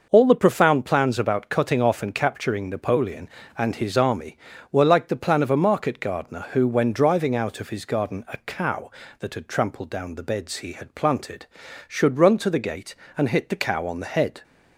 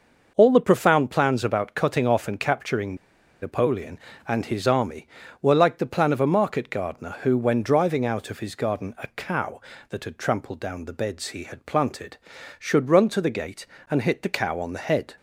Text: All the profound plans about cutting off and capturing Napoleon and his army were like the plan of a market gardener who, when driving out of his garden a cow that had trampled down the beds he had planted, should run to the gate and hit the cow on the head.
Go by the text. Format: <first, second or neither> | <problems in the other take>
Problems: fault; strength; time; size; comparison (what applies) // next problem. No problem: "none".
first | pauses between "capturing" and "Napoleon"; noticeable; at 2.9 s; 0.46 s long